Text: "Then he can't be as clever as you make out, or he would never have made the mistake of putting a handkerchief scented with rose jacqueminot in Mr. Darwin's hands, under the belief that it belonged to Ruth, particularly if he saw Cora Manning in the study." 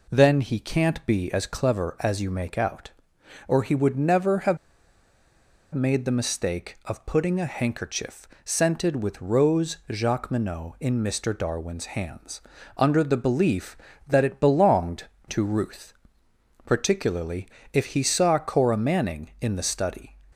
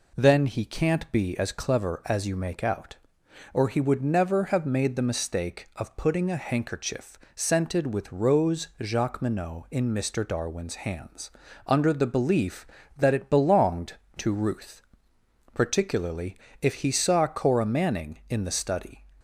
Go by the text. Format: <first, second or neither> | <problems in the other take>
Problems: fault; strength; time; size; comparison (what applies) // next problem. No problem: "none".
second | pauses between "have" and "made"; at 4.5 s; 1.1 s long // pauses between "handkerchief" and "scented"; slight; at 8.2 s; 0.16 s long; slight in the second // pauses between "particularly" and "if"; slight; at 17.4 s; 0.24 s long; slight in the second